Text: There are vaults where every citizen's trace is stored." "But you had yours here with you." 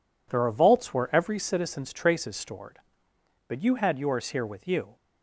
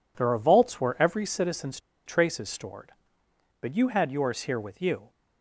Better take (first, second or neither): first